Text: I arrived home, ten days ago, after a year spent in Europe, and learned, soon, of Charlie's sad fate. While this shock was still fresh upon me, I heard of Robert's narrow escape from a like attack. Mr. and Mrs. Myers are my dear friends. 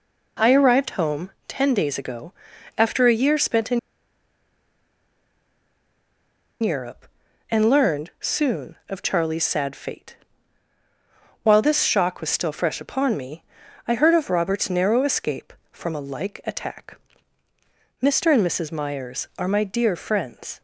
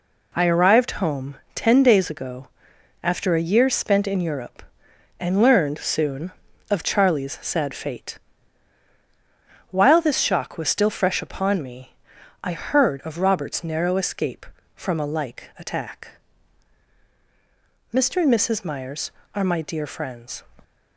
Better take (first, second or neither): second